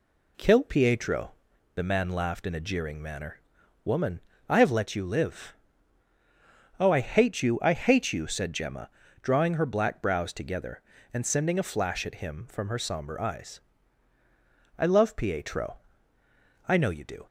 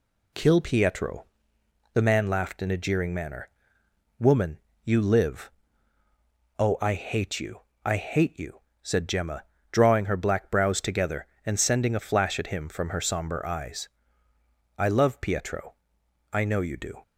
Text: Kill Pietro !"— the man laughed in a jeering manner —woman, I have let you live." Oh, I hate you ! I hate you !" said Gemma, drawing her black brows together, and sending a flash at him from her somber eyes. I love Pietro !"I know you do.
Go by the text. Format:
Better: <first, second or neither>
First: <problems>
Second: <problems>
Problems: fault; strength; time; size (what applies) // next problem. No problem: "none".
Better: first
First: none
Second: skips "I have let"; at 4.7 s